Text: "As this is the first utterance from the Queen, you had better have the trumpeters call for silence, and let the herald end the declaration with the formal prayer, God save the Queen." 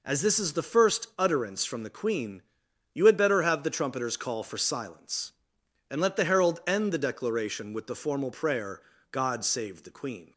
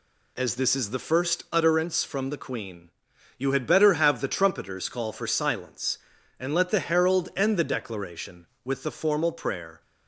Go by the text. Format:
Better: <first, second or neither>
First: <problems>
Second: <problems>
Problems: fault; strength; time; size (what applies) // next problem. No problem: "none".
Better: first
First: none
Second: stops before "God save the Queen"; at 9.8 s